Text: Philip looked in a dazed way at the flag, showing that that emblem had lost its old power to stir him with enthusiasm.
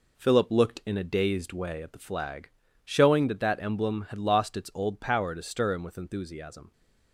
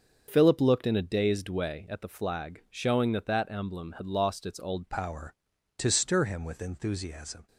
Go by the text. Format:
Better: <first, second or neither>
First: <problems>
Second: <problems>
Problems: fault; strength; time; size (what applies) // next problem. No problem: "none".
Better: first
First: none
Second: starts louder than the rest; until 1.2 s; 6.5 dB // changes voice at "power"; from 4.8 s on; 2.6 s long